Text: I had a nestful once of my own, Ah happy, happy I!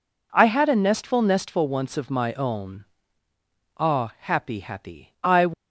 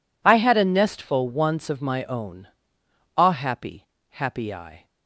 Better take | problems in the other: second | says "nestful" twice; at 1.2 s

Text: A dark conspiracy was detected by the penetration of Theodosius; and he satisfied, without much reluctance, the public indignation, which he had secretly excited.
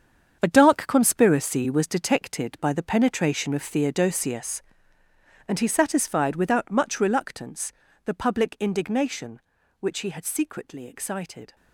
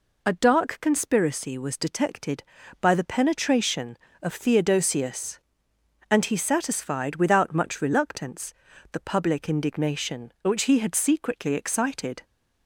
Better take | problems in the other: second | gets quieter; strong; throughout; 11 dB

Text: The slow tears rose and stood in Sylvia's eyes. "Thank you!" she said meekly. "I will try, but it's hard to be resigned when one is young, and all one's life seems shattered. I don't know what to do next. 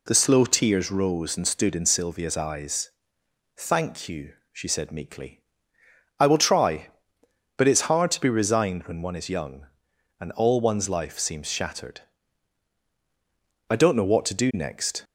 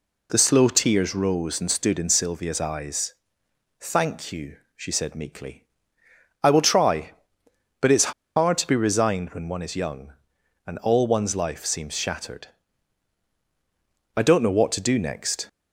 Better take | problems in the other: first | pauses between "it's" and "hard"; slight; at 8.1 s; 0.24 s long

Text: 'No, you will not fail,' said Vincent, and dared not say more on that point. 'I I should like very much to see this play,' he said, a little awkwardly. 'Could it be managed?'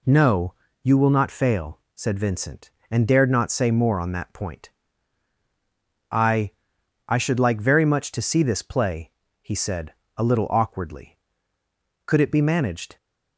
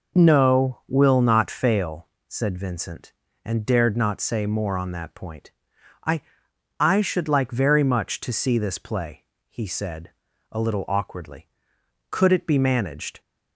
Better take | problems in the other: first | skips "you"; at 0.8 s // pauses between "I" and "I"; noticeable; at 6.2 s; 0.58 s long; noticeable in the first

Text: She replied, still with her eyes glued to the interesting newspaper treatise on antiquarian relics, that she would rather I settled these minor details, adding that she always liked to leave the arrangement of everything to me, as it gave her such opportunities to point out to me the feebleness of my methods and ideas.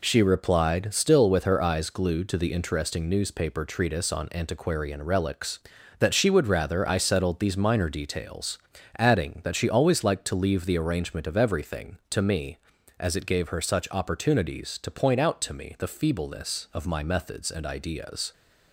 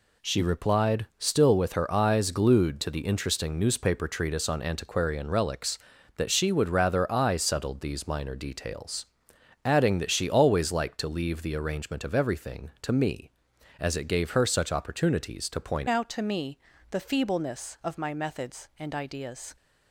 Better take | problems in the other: first | changes voice at "out"; from 15.8 s on; 3.7 s long // pauses between "me" and "the"; slight; at 16.5 s; 0.32 s long

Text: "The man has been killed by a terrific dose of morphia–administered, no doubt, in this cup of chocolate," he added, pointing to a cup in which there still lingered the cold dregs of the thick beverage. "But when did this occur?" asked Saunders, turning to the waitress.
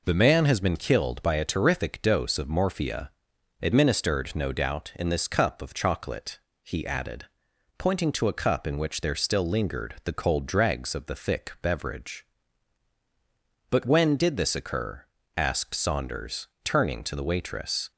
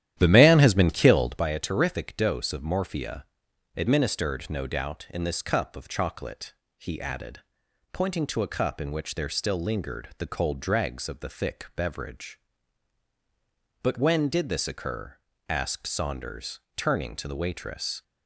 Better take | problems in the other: first | starts louder than the rest; strong; until 1.4 s; 11.5 dB

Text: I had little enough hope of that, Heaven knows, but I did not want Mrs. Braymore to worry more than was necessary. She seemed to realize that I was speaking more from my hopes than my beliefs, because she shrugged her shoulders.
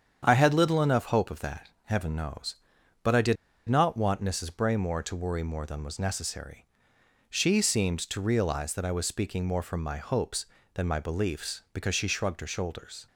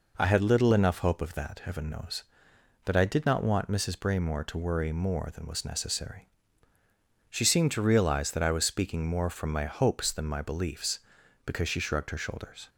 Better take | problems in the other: second | starts louder than the rest; strong; until 1.2 s; 8.5 dB // pauses between "did" and "not"; slight; at 3.3 s; 0.32 s long

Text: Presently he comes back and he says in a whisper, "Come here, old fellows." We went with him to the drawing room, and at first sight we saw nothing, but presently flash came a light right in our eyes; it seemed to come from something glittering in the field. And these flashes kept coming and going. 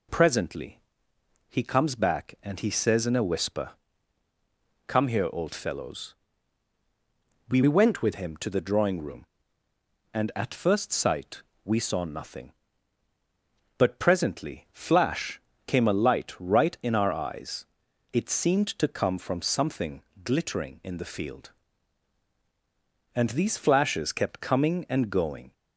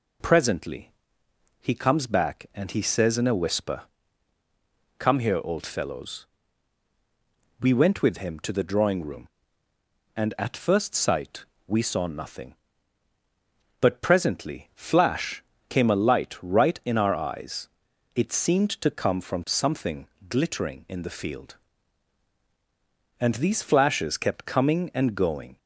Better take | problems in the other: second | pauses between "Presently" and "he"; noticeable; at 0.7 s; 0.70 s long; noticeable in the second // changes voice from "went" to "with"; from 7.6 to 8.1 s; 0.5 s long // pauses between "sight" and "we"; slight; at 11.4 s; 0.22 s long; slight in the second // pauses between "flash" and "came"; slight; at 15.4 s; 0.26 s long; slight in the second // pauses between "something" and "glittering"; slight; at 20.0 s; 0.22 s long; slight in the second

